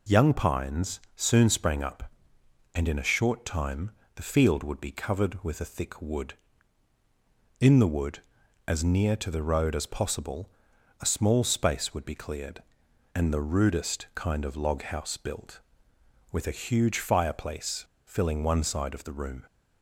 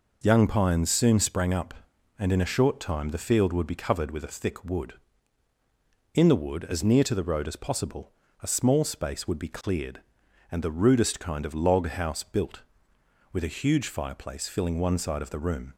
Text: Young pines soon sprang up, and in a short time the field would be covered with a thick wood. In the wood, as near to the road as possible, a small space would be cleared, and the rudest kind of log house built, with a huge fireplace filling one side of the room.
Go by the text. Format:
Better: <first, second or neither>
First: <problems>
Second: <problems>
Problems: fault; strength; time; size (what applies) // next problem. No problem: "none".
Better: second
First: pauses between "pines" and "soon"; slight; at 1.0 s; 0.16 s long // pauses between "time" and "the"; slight; at 3.9 s; 0.24 s long // pauses between "fireplace" and "filling"; slight; at 17.8 s; 0.23 s long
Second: none